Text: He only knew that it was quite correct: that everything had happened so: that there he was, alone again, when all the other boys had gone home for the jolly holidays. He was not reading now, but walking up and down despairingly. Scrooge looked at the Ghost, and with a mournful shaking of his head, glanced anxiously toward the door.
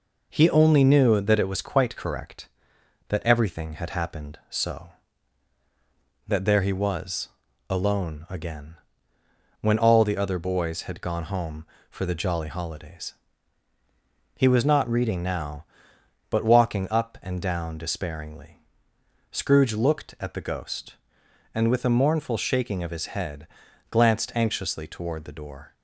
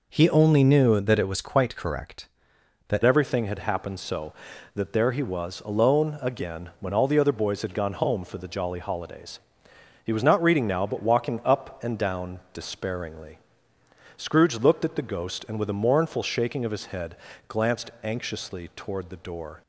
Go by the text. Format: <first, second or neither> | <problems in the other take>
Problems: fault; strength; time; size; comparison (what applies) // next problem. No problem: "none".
first | changes voice at "everything"; from 3.0 s on; 16.6 s long